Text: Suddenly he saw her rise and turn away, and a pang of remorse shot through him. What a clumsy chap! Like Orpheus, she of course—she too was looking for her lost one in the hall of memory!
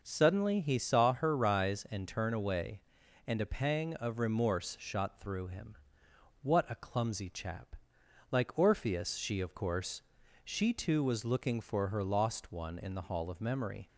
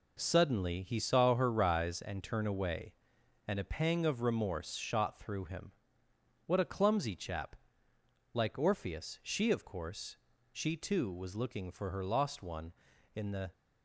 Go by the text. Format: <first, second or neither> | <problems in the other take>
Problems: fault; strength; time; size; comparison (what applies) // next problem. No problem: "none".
first | stops before "hall of memory"; at 13.5 s